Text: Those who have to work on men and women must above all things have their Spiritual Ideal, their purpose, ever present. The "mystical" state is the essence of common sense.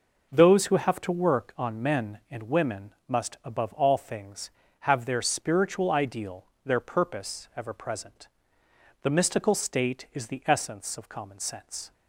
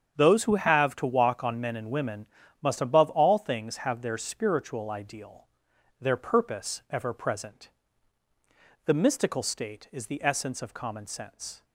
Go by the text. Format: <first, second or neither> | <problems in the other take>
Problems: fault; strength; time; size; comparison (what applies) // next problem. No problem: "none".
first | starts louder than the rest; strong; until 1.1 s; 8 dB // says "walk" for "work"; at 1.0 s // pauses between "women" and "must"; slight; at 2.2 s; 0.34 s long